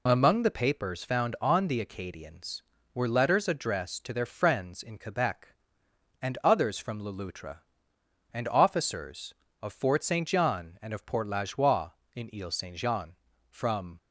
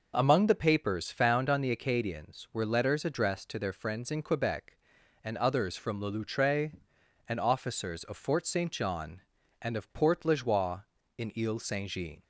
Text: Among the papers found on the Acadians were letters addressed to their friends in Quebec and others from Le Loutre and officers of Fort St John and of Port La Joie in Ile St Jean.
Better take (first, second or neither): second